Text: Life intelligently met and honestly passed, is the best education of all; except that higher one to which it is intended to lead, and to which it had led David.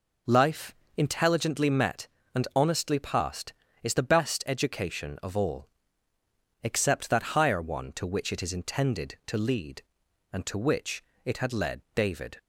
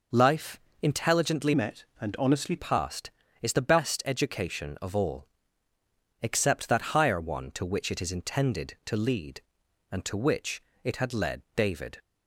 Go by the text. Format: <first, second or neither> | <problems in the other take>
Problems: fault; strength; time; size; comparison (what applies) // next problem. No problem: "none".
first | pauses between "Life" and "intelligently"; slight; at 0.6 s; 0.22 s long; slight in the first // changes voice from "met" to "honestly"; from 1.5 to 2.5 s; 1.0 s long // pauses between "which" and "it"; slight; at 10.6 s; 0.22 s long; slight in the first